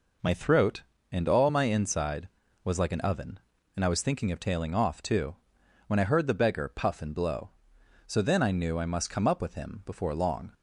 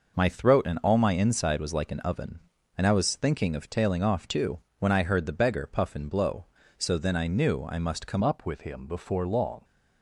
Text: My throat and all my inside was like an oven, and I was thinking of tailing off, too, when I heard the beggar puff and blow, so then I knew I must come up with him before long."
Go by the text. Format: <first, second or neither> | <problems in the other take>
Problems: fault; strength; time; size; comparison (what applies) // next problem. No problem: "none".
first | changes voice at "up"; from 8.2 s on; 1.4 s long